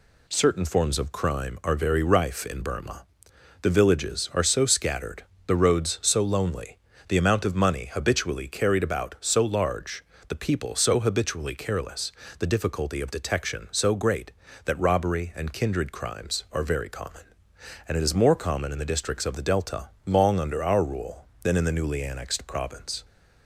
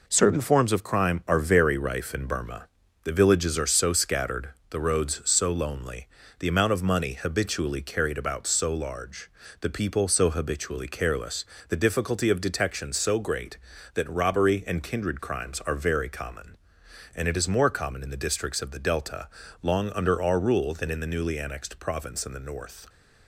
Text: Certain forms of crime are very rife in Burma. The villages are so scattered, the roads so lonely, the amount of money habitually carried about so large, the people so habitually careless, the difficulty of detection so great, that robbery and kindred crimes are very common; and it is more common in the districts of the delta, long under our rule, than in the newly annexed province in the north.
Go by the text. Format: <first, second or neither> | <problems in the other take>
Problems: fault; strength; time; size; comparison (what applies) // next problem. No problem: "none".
second | stops before "in the north"; at 23.0 s